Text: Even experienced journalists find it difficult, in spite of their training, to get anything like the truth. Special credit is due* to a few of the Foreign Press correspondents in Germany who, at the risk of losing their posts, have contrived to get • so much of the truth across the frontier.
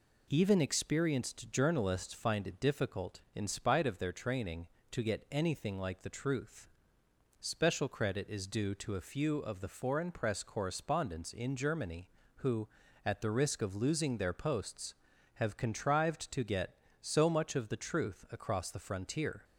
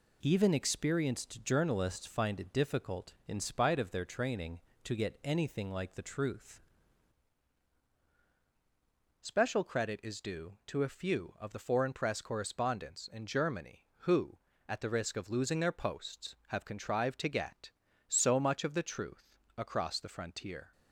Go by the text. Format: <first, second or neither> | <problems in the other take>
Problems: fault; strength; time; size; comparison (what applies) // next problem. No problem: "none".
first | changes voice at "Special"; from 9.2 s on; 11.5 s long // pauses between "truth" and "across"; slight; at 19.3 s; 0.18 s long